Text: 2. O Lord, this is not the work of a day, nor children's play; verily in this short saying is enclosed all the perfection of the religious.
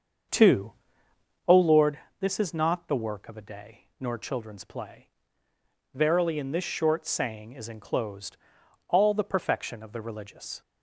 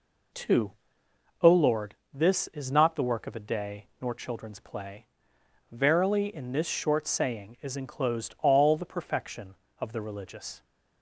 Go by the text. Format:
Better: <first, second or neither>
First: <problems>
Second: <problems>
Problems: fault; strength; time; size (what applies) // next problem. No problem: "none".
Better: second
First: starts louder than the rest; until 2.0 s; 7 dB // pauses between "enclosed" and "all"; noticeable; at 8.3 s; 0.52 s long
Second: none